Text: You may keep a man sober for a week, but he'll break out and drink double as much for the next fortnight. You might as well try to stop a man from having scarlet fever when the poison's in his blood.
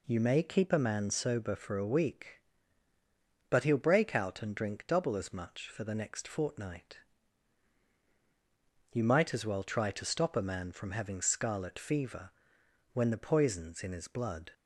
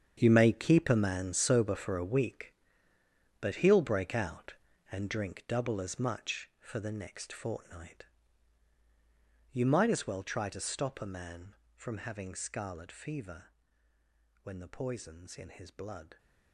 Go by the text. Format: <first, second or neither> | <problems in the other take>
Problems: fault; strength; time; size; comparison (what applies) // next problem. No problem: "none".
first | gets quieter; strong; throughout; 13.5 dB // pauses between "fever" and "when"; noticeable; at 13.4 s; 0.98 s long; noticeable in the first